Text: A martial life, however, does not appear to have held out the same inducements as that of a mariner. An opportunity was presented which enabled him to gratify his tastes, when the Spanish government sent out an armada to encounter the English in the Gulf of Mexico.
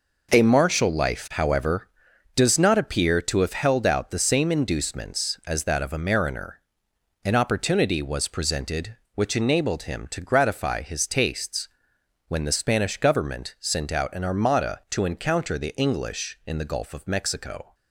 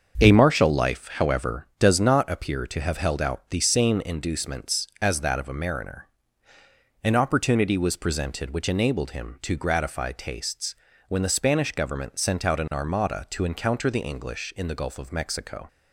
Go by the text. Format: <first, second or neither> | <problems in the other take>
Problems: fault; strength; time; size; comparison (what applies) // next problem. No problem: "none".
first | starts louder than the rest; until 1.1 s; 6.5 dB // skips "his"; at 10.1 s